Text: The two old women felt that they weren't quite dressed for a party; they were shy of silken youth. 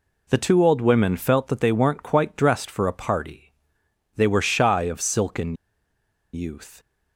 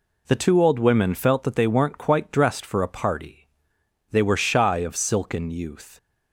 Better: second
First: pauses between "silken" and "youth"; noticeable; at 5.5 s; 0.80 s long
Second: none

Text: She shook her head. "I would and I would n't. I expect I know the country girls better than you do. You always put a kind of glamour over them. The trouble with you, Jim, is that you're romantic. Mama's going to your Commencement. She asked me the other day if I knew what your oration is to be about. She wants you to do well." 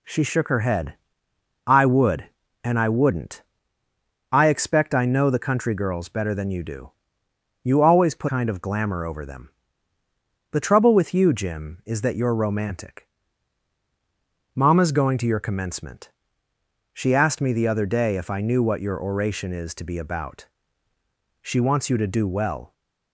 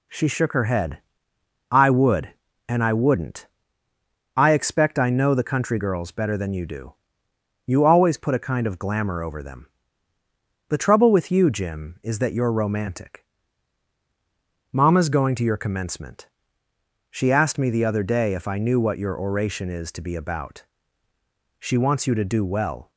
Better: second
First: skips "a"; at 8.2 s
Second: none

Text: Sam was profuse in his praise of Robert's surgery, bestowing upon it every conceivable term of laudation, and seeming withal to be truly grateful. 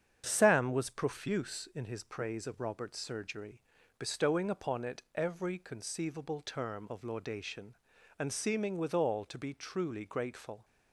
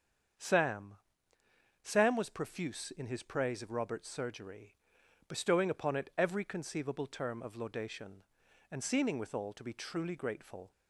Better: first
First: starts louder than the rest; strong; until 1.2 s; 8 dB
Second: starts louder than the rest; strong; until 2.2 s; 7.5 dB // says "Sam" twice; at 1.8 s

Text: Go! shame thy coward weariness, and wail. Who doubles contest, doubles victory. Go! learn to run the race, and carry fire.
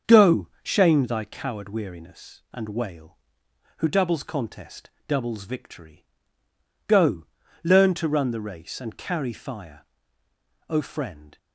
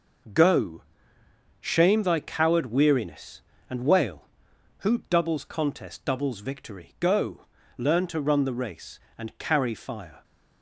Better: second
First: starts louder than the rest; until 1.2 s; 6.5 dB // goes on to say "O Friend"; noticeable; from 10.6 s on; 0.68 s long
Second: none

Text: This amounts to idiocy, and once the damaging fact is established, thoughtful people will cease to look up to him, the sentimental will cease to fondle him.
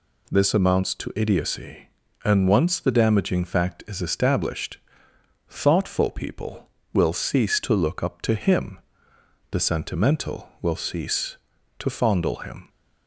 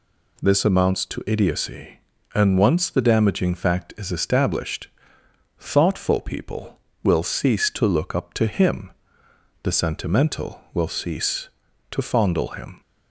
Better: neither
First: none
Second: none

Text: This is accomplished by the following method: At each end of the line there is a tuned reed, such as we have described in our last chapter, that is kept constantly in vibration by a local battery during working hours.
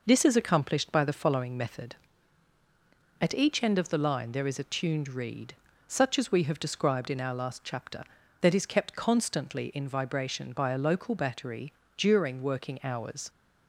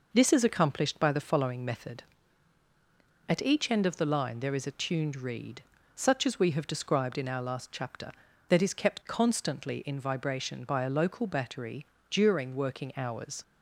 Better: neither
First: pauses between "battery" and "during"; slight; at 11.7 s; 0.26 s long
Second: pauses between "battery" and "during"; slight; at 11.8 s; 0.26 s long

